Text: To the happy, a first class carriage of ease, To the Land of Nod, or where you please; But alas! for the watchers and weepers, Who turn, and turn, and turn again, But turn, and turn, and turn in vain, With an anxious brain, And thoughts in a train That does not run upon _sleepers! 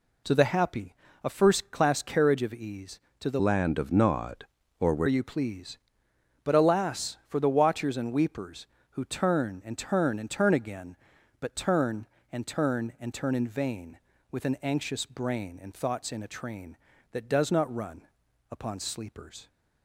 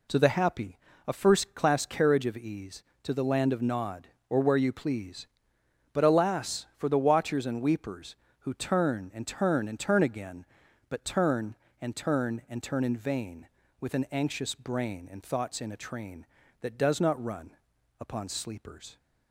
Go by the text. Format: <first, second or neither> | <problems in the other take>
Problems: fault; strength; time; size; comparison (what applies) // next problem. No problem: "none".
second | changes voice from "Land" to "where"; from 3.3 to 5.0 s; 1.7 s long // pauses between "run" and "upon"; at 18.0 s; 0.42 s long; also in the second